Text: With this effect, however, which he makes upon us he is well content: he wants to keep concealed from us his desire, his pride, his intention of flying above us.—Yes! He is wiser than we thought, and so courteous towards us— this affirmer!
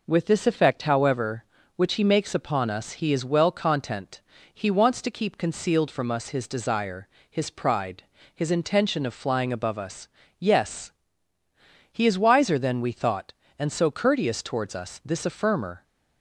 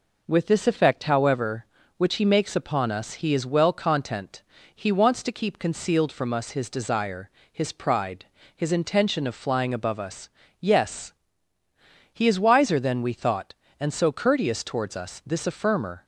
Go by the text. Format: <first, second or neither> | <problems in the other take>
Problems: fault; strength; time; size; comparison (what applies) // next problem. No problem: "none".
neither | none